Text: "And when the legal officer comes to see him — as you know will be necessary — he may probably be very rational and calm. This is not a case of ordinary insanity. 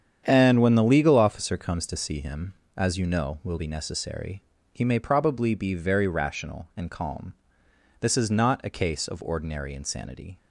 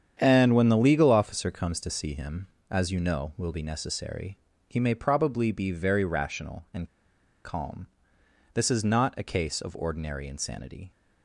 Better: first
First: starts louder than the rest; strong; until 1.2 s; 8.5 dB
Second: starts louder than the rest; strong; until 1.2 s; 8.5 dB // pauses between "and" and "calm"; noticeable; at 6.8 s; 0.56 s long

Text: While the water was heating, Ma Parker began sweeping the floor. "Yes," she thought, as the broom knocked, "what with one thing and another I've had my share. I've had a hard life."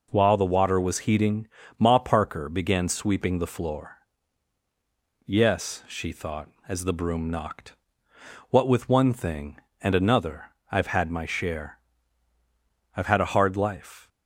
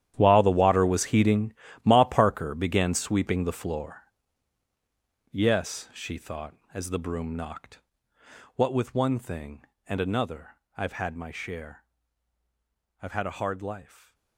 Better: first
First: pauses between "another" and "I've"; slight; at 10.5 s; 0.18 s long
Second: gets quieter; strong; throughout; 15.5 dB // pauses between "another" and "I've"; slight; at 10.5 s; 0.18 s long

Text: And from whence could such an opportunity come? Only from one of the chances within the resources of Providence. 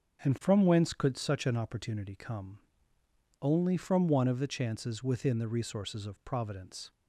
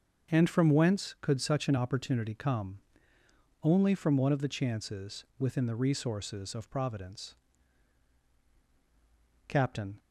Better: first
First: starts louder than the rest; until 1.2 s; 6.5 dB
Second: starts louder than the rest; until 1.3 s; 6.5 dB // goes on to say "Captain"; from 9.4 s on; 0.50 s long

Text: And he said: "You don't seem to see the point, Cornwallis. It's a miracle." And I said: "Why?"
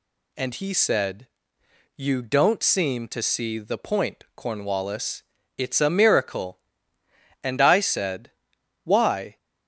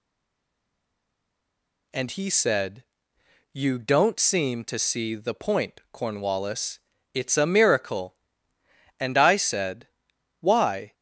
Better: first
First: none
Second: stays silent before the first word; noticeable; until 1.9 s; 1.9 s long

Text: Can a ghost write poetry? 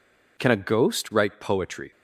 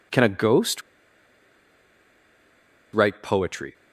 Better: first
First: none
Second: pauses between "ghost" and "write"; strong; at 0.8 s; 2.1 s long

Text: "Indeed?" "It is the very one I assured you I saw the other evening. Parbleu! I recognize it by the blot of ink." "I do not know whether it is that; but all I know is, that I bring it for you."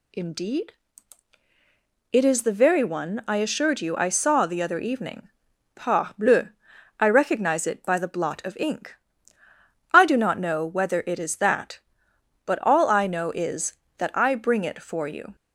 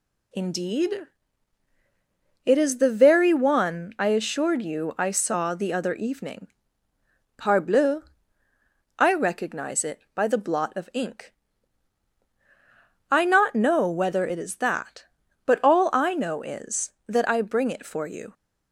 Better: first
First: none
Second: skips "do"; at 13.2 s

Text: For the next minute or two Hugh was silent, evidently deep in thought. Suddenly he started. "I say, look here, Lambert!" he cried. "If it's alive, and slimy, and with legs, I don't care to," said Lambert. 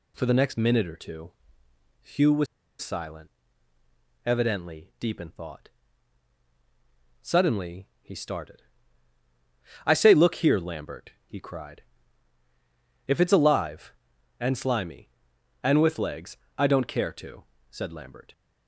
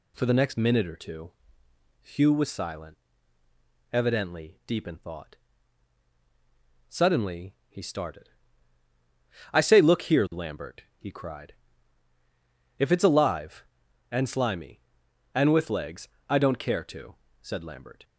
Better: second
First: pauses between "two" and "Hugh"; noticeable; at 1.3 s; 0.70 s long // pauses between "was" and "silent"; slight; at 2.4 s; 0.35 s long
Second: pauses between "two" and "Hugh"; noticeable; at 1.3 s; 0.70 s long

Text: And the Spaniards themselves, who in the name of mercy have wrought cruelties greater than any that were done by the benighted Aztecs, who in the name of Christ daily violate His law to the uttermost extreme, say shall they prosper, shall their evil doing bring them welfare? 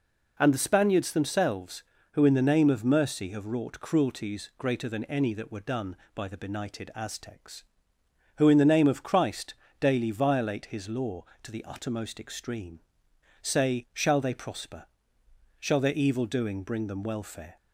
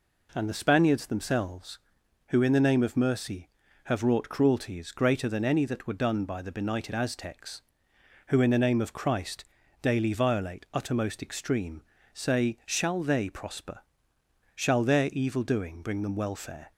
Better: first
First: pauses between "Christ" and "daily"; slight; at 9.5 s; 0.24 s long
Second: pauses between "Christ" and "daily"; slight; at 9.4 s; 0.36 s long // skips "His law to the"; at 10.6 s

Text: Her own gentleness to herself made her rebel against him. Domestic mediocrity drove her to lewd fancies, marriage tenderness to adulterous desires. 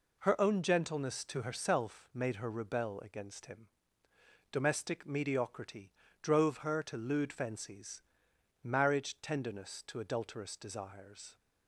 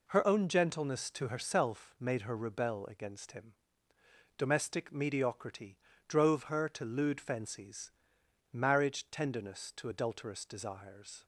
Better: neither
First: pauses between "mediocrity" and "drove"; slight; at 5.9 s; 0.32 s long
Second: pauses between "mediocrity" and "drove"; slight; at 5.7 s; 0.32 s long

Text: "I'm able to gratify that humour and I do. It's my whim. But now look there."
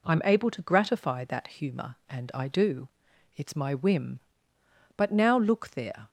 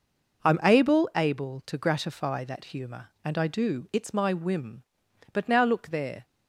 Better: first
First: none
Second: says "able" twice; at 1.1 s

